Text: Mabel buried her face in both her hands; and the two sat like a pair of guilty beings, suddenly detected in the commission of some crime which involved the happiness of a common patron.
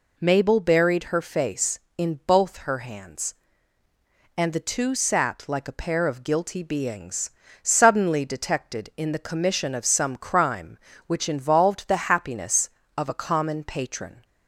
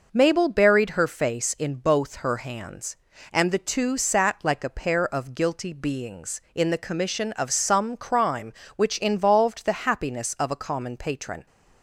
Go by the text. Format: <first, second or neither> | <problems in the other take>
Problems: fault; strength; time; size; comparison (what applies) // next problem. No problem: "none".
first | skips "suddenly detected"; at 6.4 s